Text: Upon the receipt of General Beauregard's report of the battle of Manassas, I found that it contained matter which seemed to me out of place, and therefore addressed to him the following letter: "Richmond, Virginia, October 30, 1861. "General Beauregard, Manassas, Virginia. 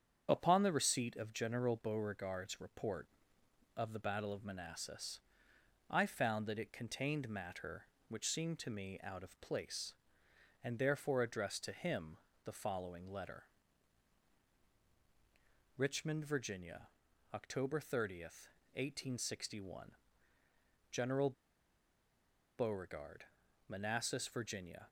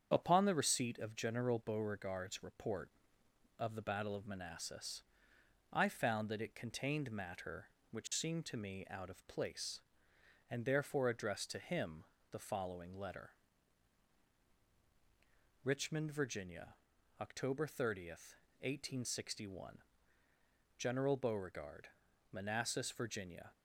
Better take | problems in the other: second | starts louder than the rest; strong; until 1.3 s; 7.5 dB; strong in the second // pauses between "him" and "the"; slight; at 12.1 s; 0.26 s long; slight in the second // pauses between "General" and "Beauregard"; strong; at 21.3 s; 1.2 s long

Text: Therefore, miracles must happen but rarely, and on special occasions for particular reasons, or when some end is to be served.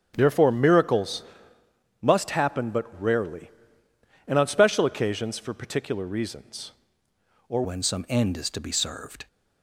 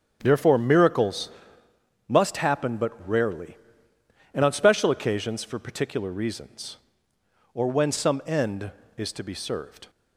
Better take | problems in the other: second | starts louder than the rest; strong; until 1.1 s; 8.5 dB; strong in the second // pauses between "miracles" and "must"; noticeable; at 1.2 s; 0.78 s long; noticeable in the second // changes voice at "when"; from 7.6 s on; 1.6 s long

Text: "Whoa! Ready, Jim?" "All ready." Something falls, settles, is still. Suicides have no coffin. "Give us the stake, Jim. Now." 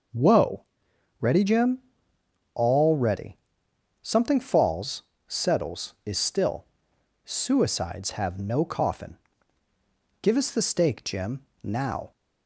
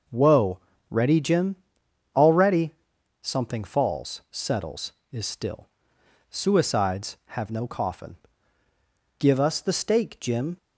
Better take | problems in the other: first | stops before "Now"; at 10.5 s

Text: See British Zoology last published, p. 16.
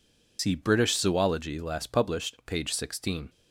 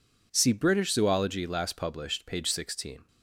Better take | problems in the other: second | loses the start of "See"; at 0.3 s; 110 ms

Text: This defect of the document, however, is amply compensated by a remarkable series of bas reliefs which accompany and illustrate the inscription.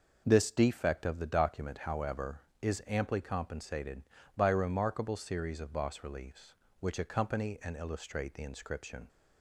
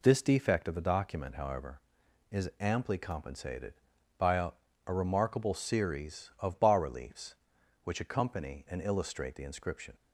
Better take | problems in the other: first | says "a" twice; at 4.8 s

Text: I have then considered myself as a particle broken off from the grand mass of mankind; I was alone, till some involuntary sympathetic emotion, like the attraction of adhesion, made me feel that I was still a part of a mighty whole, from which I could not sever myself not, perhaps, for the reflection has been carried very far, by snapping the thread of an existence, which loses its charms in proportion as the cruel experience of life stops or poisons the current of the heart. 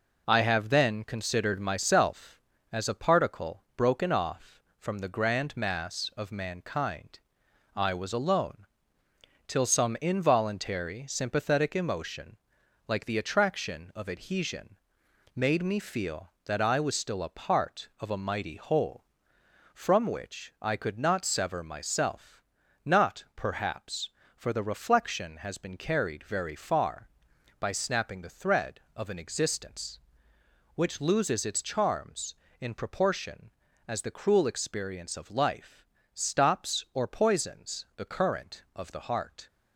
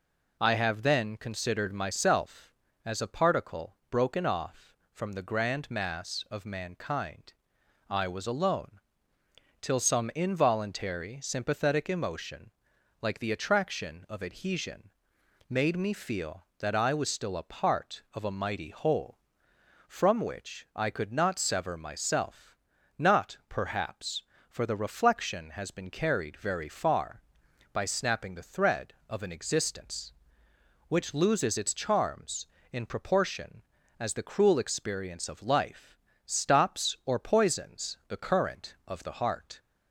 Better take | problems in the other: second | gets quieter; noticeable; throughout; 4.5 dB // pauses between "myself" and "not"; noticeable; at 22.3 s; 0.46 s long; also in the second // pauses between "life" and "stops"; slight; at 35.8 s; 0.28 s long; slight in the second

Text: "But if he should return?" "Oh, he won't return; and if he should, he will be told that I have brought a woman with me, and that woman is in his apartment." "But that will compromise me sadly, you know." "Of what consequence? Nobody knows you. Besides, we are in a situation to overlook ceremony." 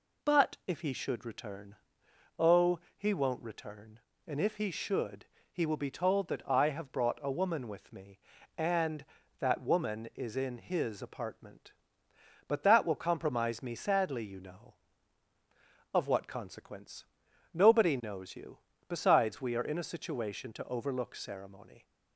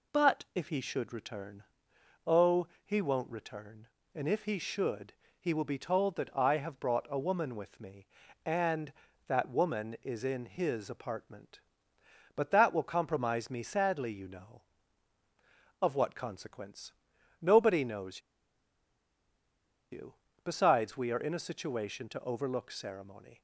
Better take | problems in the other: first | pauses between "knows" and "you"; strong; at 18.1 s; 1.7 s long

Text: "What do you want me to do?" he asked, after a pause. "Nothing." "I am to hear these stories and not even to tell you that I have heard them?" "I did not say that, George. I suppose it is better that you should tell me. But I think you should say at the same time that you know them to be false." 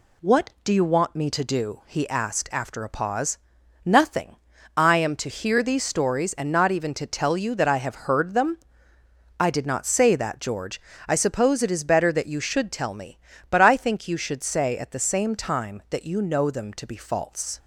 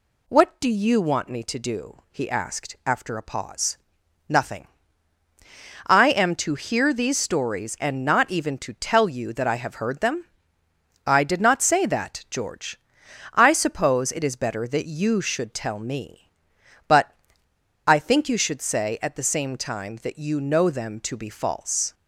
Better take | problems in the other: first | pauses between "But" and "I"; noticeable; at 17.1 s; 0.74 s long

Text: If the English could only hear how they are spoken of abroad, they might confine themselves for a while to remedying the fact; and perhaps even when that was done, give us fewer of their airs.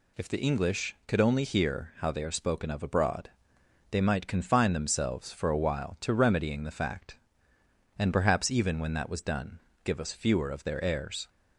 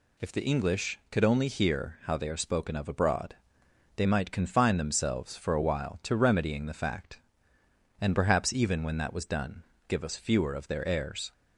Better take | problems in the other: neither | none

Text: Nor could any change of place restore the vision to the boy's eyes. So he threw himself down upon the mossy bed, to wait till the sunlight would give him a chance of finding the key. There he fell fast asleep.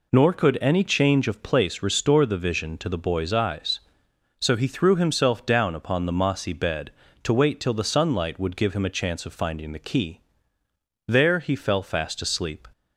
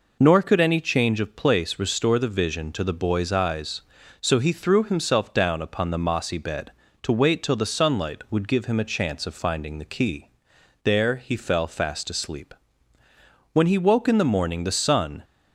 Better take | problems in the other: first | goes on to say "When he woke in the morning the sun"; strong; from 13.5 s on; 1.7 s long

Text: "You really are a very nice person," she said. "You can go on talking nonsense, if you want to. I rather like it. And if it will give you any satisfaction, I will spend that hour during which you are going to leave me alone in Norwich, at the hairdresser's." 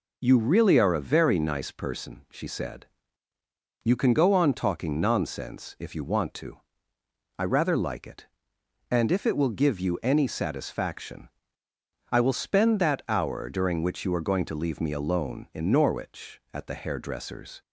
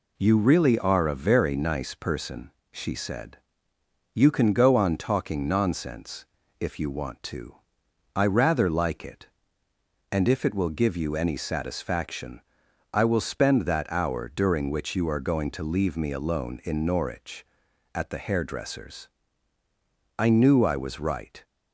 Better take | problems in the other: first | goes on to say "I knew I was right"; noticeable; from 20.1 s on; 1.2 s long

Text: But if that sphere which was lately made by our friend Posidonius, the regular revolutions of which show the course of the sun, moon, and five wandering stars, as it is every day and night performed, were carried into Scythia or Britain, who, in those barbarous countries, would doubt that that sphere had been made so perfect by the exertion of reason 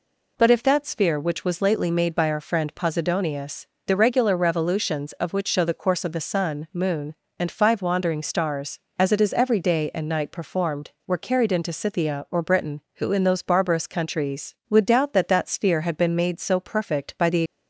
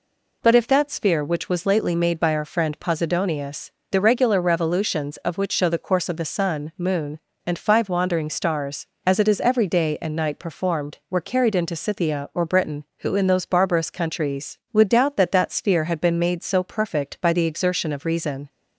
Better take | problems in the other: second | stops before "exertion of reason"; at 17.4 s

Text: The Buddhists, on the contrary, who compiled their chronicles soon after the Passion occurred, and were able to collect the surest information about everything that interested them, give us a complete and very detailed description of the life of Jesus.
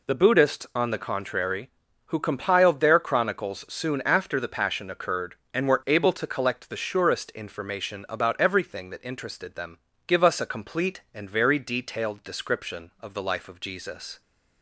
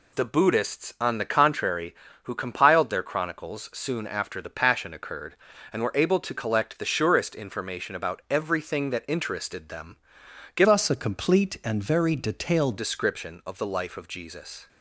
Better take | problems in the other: first | changes voice from "us" to "detailed"; from 10.6 to 12.7 s; 2.1 s long

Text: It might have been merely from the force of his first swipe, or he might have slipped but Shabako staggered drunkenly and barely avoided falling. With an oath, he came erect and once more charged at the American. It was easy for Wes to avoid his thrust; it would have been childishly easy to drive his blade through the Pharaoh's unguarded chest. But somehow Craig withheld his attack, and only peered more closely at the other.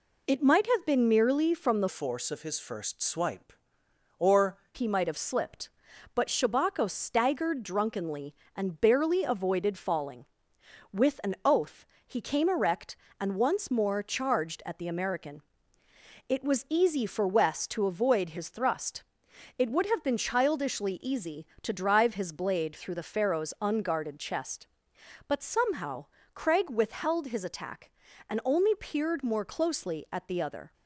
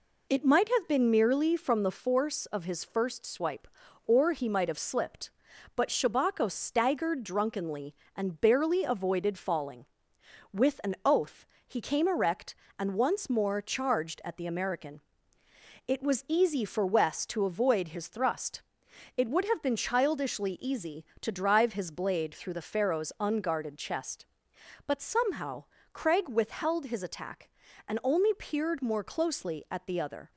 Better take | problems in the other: second | changes voice from "force" to "or"; from 1.8 to 4.5 s; 2.7 s long // pauses between "somehow" and "Craig"; slight; at 26.0 s; 0.30 s long; slight in the second

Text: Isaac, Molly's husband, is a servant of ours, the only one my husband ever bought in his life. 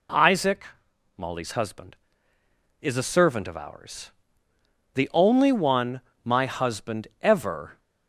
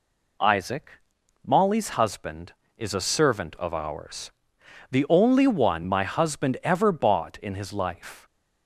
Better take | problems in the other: second | pauses between "one" and "my"; slight; at 6.0 s; 0.24 s long // stops before "bought in his life"; at 7.7 s

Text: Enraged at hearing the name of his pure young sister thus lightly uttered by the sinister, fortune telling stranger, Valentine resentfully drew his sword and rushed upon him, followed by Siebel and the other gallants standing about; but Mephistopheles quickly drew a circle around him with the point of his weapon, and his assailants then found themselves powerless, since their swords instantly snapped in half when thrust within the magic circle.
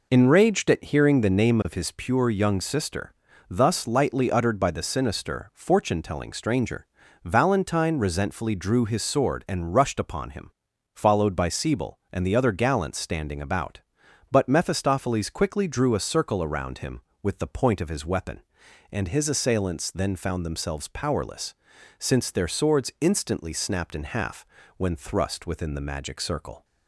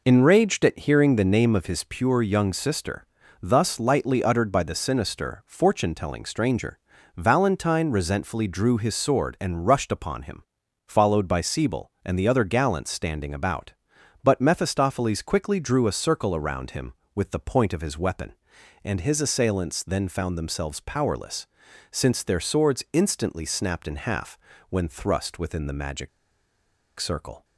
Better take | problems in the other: first | pauses between "sister" and "thus"; at 3.0 s; 0.38 s long; also in the first // pauses between "half" and "when"; slight; at 24.3 s; 0.32 s long; slight in the first // pauses between "magic" and "circle"; noticeable; at 26.0 s; 0.89 s long

